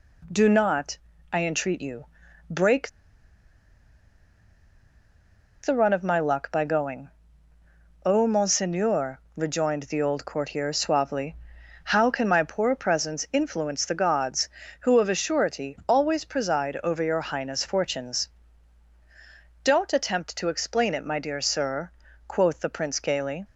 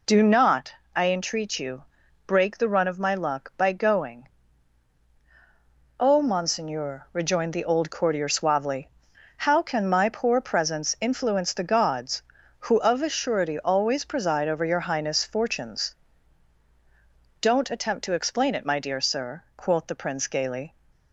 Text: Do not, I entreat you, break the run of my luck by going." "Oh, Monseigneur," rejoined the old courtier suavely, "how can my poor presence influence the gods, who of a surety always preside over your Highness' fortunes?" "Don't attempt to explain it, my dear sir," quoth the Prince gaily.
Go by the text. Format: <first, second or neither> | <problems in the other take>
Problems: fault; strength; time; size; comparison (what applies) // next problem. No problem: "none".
second | pauses between "break" and "the"; strong; at 2.8 s; 2.7 s long